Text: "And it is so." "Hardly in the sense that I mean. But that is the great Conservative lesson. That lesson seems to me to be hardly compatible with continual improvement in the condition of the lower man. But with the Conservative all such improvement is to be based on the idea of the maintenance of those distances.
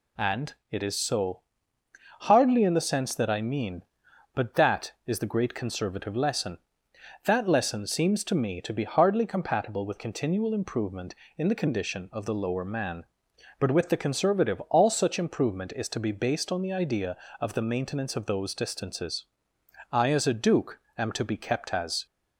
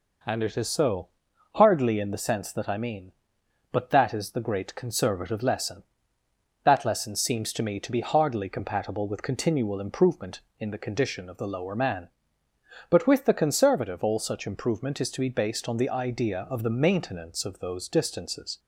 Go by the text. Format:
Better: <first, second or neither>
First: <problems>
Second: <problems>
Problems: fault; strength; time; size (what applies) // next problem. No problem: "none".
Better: second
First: pauses between "And" and "it"; slight; at 0.5 s; 0.16 s long // goes on to say "I as a Duke am to be kept as"; strong; from 19.9 s on; 2.1 s long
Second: none